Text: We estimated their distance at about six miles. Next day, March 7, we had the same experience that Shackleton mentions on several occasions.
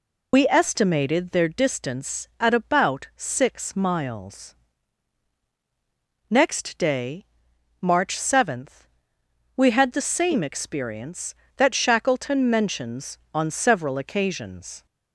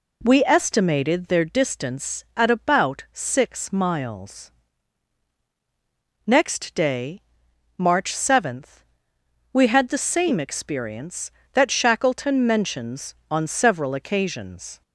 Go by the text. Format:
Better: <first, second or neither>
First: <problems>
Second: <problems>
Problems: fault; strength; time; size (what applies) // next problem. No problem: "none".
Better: second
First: loses the start of "We"; at 0.3 s; 90 ms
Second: none